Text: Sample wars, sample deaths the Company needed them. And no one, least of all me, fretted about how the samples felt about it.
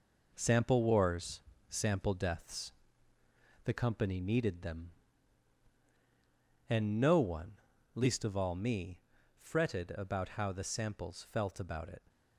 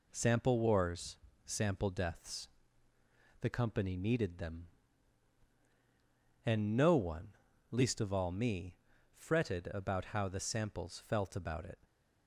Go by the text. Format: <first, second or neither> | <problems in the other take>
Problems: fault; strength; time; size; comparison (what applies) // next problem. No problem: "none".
second | gets quieter; noticeable; throughout; 5.5 dB // pauses between "deaths" and "the"; noticeable; at 2.7 s; 0.92 s long; noticeable in the second